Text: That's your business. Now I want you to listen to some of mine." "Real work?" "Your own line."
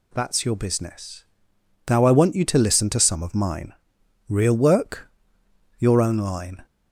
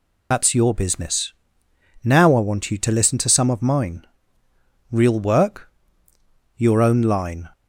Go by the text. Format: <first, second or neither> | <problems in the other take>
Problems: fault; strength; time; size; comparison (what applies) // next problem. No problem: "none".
first | loses the start of "That's"; at 0.3 s; 50 ms